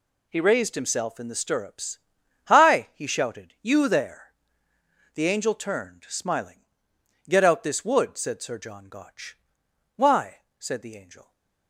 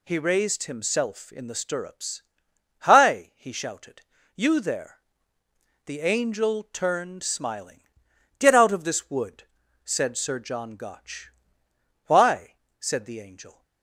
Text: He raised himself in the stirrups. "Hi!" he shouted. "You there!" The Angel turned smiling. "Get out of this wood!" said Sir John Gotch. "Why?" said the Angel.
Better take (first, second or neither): second